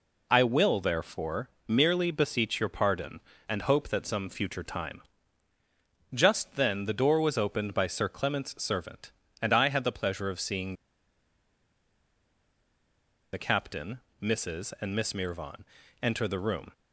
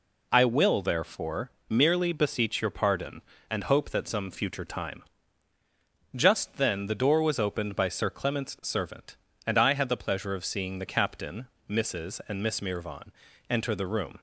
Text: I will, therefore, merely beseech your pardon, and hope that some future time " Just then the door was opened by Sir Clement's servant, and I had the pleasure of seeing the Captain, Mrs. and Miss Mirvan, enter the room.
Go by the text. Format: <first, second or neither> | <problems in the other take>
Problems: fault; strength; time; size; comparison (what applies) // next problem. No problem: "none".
second | pauses between "seeing" and "the"; strong; at 10.7 s; 2.6 s long